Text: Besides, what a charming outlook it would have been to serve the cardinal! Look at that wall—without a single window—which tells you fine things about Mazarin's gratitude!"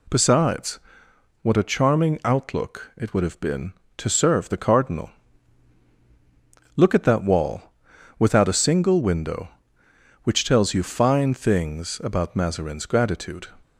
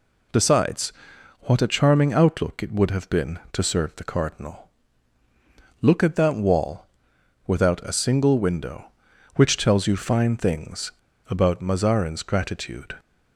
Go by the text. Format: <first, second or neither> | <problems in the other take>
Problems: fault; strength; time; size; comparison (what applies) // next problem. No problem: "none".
first | pauses between "things" and "about"; at 10.9 s; 0.39 s long